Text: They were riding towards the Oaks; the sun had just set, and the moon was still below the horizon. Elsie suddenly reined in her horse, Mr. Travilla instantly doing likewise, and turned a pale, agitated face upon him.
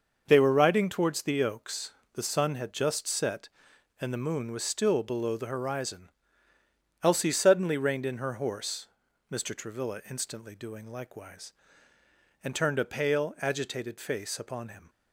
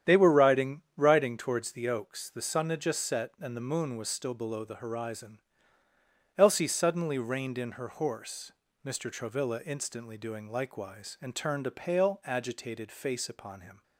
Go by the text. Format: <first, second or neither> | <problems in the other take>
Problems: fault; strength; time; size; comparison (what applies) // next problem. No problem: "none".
first | starts louder than the rest; strong; until 1.2 s; 9.5 dB; noticeable in the first // says "riding" twice; at 0.9 s